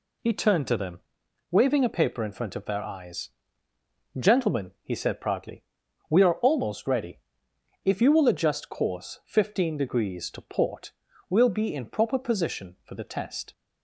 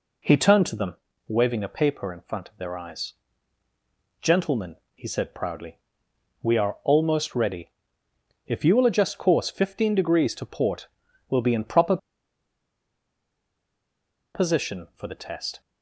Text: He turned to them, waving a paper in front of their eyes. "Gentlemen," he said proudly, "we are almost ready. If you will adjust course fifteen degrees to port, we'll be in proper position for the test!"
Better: first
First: none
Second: pauses between "proper" and "position"; strong; at 11.9 s; 2.3 s long

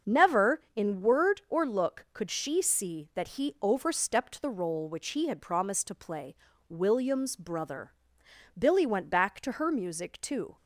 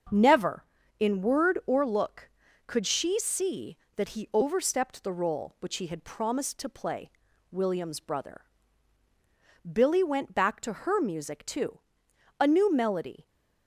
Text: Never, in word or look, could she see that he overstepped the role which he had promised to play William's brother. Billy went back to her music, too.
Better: first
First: starts louder than the rest; until 1.2 s; 7 dB // pauses between "play" and "William's"; slight; at 6.3 s; 0.34 s long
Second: starts louder than the rest; until 1.4 s; 7 dB // pauses between "play" and "William's"; at 7.0 s; 0.42 s long // goes on to say "A new melody"; noticeable; from 12.3 s on; 0.88 s long

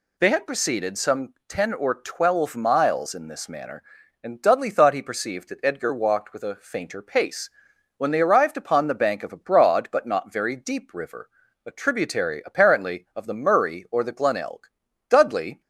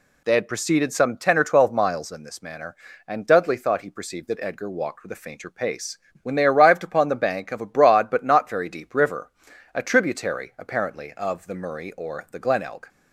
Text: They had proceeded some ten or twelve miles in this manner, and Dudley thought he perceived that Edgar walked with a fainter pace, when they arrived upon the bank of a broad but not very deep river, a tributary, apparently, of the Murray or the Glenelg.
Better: second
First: goes on to say "Dudley"; from 15.0 s on; 0.52 s long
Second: none

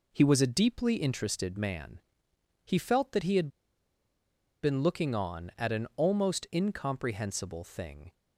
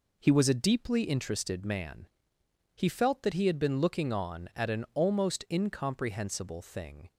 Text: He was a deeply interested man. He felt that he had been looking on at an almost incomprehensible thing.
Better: second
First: pauses between "had" and "been"; at 3.4 s; 1.1 s long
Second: none

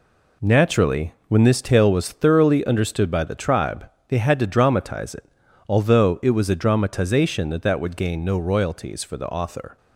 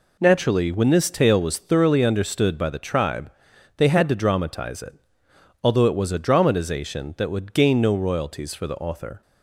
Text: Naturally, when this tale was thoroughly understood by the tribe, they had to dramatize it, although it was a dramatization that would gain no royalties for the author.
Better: second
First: says "that" twice; at 7.6 s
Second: none

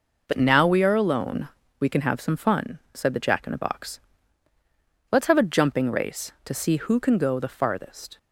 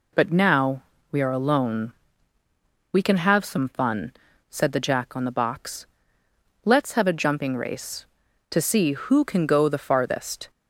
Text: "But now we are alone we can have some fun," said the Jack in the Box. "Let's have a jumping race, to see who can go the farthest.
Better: first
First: pauses between "alone" and "we"; slight; at 1.4 s; 0.28 s long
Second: pauses between "now" and "we"; slight; at 0.8 s; 0.26 s long // pauses between "alone" and "we"; at 1.9 s; 1.0 s long // says "on" for "in"; at 5.1 s

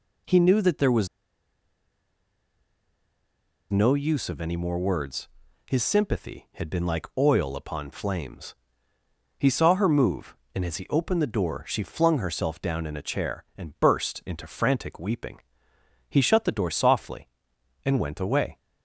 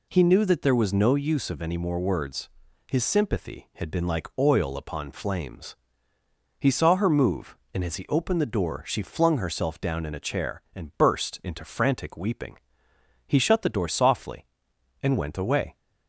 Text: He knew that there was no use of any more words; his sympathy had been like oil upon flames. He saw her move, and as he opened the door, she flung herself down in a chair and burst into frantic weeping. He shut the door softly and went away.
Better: second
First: pauses between "was" and "no"; strong; at 1.0 s; 2.6 s long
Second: none

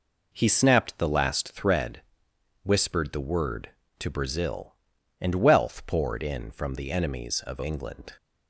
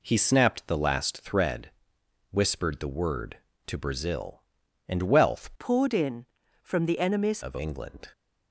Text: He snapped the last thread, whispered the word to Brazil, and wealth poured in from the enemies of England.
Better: first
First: none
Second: changes voice from "poured" to "enemies"; from 5.5 to 7.4 s; 1.9 s long

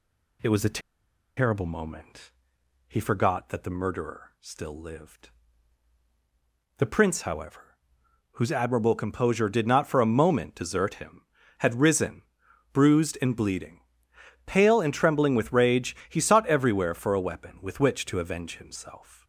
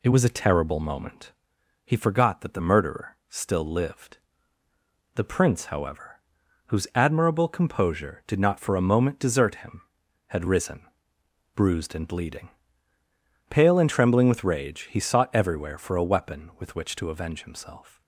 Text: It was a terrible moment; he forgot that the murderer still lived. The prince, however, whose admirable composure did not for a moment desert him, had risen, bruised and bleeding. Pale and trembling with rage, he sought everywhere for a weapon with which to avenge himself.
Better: second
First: pauses between "a" and "terrible"; noticeable; at 0.8 s; 0.56 s long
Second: none

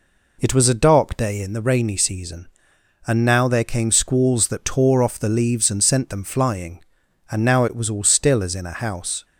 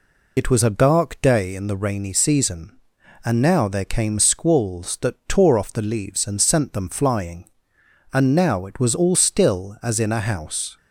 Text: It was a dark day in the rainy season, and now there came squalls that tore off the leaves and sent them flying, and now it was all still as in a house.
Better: first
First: none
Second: loses the start of "It"; at 0.3 s; 45 ms

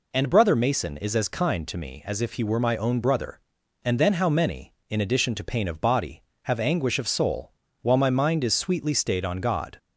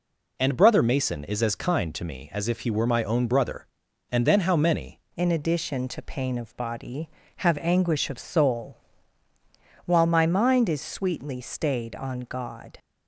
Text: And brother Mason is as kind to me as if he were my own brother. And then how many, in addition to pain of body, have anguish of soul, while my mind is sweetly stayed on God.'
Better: first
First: none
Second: changes voice at "in"; from 5.1 s on; 7.6 s long

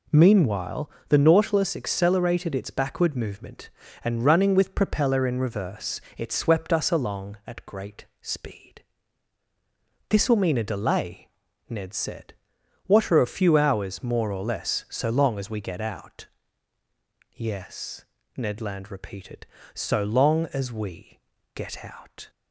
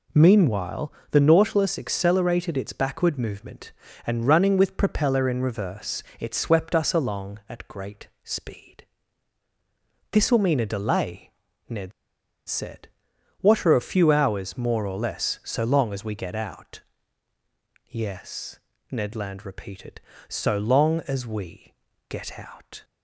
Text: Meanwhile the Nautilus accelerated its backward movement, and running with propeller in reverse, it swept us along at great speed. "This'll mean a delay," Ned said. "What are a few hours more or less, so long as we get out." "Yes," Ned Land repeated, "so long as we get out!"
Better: first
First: pauses between "Meanwhile" and "the"; slight; at 0.8 s; 0.20 s long // pauses between "great" and "speed"; slight; at 8.0 s; 0.16 s long // pauses between "we" and "get"; slight; at 21.1 s; 0.34 s long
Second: pauses between "Meanwhile" and "the"; slight; at 0.9 s; 0.20 s long // pauses between "great" and "speed"; slight; at 8.0 s; 0.16 s long // pauses between "Ned" and "said"; noticeable; at 11.9 s; 0.56 s long // pauses between "we" and "get"; slight; at 21.7 s; 0.34 s long

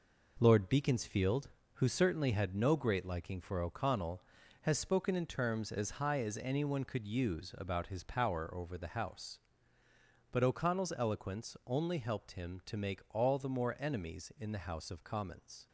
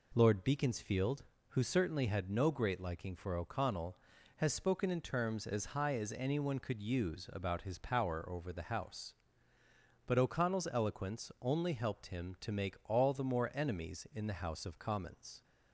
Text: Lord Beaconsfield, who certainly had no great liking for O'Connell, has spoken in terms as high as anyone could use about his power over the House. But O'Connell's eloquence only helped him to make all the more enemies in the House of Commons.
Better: second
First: gets quieter; throughout; 7 dB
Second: none

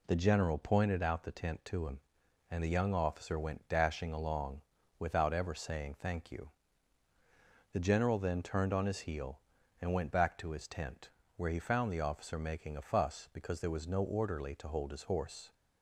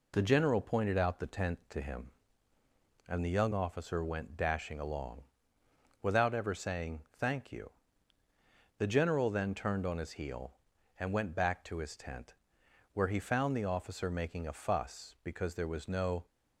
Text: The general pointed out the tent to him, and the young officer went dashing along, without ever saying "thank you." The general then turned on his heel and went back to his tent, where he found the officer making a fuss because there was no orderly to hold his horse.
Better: first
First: none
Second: stops before "orderly to hold his horse"; at 16.2 s

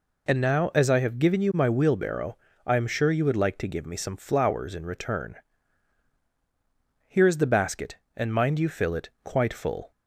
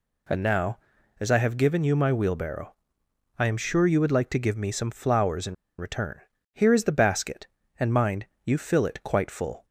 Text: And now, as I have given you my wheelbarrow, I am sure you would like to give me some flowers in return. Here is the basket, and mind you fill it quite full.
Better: first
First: none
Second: pauses between "in" and "return"; slight; at 5.5 s; 0.23 s long // pauses between "mind" and "you"; slight; at 8.2 s; 0.18 s long

